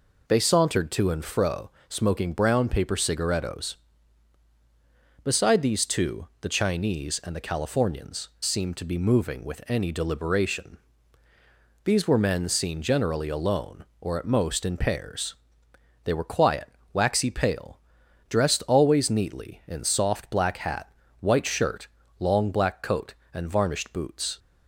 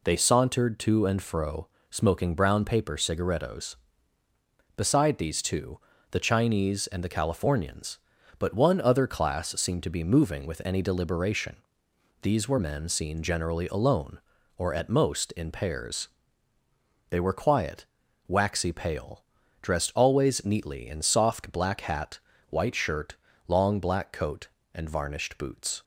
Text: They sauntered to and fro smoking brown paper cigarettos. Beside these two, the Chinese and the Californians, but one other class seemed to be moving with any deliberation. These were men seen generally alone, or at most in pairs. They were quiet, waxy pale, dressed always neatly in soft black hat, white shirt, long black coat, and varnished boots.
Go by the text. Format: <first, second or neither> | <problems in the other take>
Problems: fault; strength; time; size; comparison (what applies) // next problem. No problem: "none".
second | pauses between "fro" and "smoking"; slight; at 1.6 s; 0.18 s long; slight in the second // skips "but one other class"; at 8.3 s